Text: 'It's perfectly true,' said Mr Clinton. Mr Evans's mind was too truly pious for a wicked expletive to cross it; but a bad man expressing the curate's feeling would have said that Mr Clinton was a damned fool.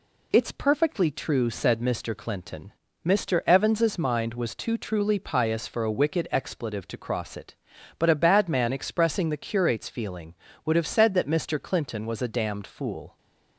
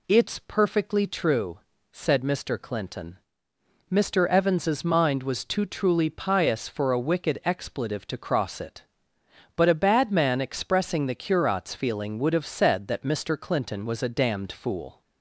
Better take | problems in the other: neither | none

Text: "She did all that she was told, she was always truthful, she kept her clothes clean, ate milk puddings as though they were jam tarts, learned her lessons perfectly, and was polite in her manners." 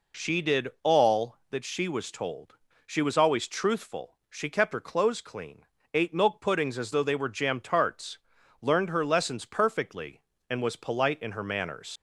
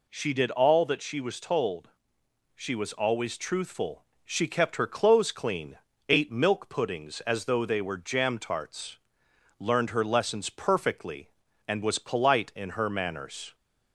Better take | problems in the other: second | leaves "manners" unfinished; at 11.9 s; 85 ms

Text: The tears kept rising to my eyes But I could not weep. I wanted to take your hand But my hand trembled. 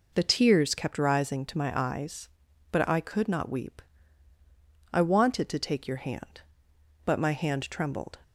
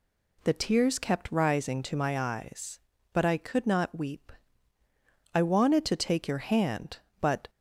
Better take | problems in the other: first | stops before "my hand trembled"; at 7.4 s

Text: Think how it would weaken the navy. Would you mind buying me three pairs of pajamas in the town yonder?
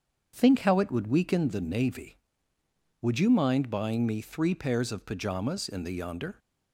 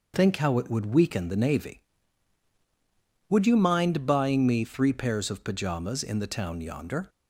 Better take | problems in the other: second | starts louder than the rest; strong; until 1.3 s; 7 dB // skips "town"; at 5.9 s

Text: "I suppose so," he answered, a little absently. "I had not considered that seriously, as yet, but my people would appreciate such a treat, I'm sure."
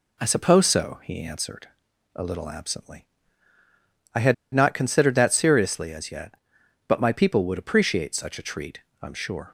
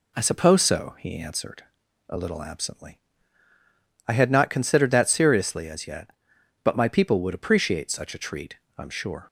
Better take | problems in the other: second | pauses between "had" and "not"; slight; at 4.3 s; 0.20 s long

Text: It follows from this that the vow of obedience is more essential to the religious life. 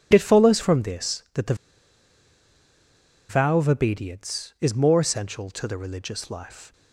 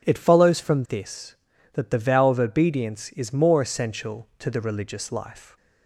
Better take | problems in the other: second | pauses between "the" and "vow"; strong; at 1.5 s; 1.7 s long

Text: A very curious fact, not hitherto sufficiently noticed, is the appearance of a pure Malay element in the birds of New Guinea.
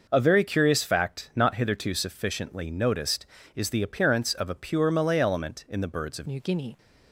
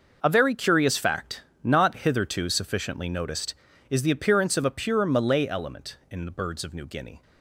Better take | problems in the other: second | changes voice at "New"; from 6.2 s on; 0.5 s long

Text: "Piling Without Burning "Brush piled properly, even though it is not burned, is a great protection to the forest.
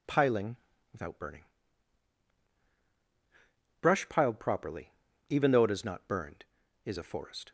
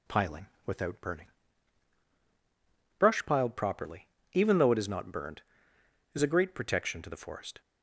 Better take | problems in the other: second | pauses between "Piling" and "Without"; slight; at 0.5 s; 0.34 s long; slight in the second // pauses between "Burning" and "Brush"; strong; at 1.4 s; 2.3 s long; strong in the second // skips "great protection to the"; at 7.0 s

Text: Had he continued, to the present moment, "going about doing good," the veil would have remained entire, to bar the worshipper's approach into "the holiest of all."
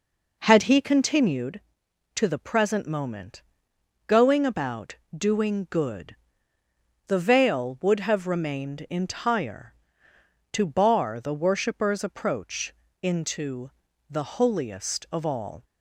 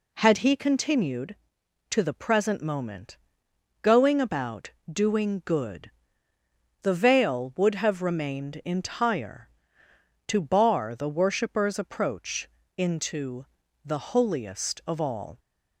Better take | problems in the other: second | starts louder than the rest; noticeable; until 1.6 s; 4.5 dB // pauses between "about" and "doing"; slight; at 4.9 s; 0.22 s long; slight in the second // pauses between "approach" and "into"; slight; at 12.7 s; 0.30 s long; slight in the second // pauses between "into" and "the"; slight; at 13.7 s; 0.36 s long; slight in the second

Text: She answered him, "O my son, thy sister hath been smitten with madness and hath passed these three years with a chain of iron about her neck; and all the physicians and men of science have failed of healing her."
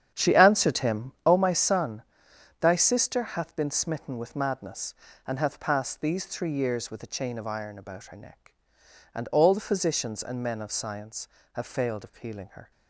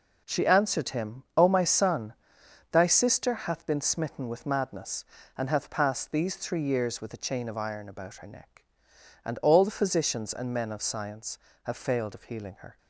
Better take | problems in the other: second | starts louder than the rest; strong; until 1.3 s; 8.5 dB

